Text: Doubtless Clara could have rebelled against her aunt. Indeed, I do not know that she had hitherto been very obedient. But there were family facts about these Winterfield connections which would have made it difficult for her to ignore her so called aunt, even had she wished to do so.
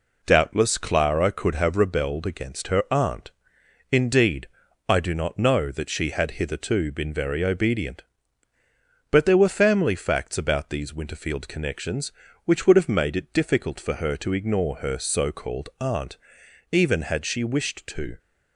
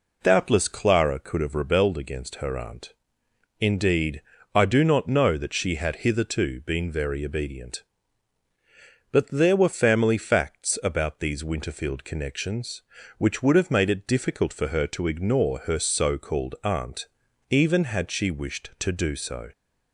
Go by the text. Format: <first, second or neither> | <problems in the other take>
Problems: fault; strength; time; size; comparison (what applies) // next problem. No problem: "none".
second | stops before "do so"; at 18.1 s